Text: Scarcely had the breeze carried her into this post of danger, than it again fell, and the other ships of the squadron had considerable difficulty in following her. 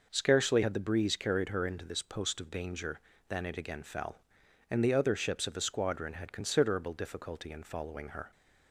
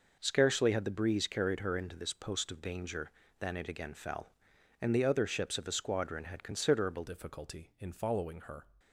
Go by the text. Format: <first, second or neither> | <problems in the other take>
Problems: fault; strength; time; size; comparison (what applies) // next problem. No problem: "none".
first | changes voice at "difficulty"; from 7.0 s on; 1.6 s long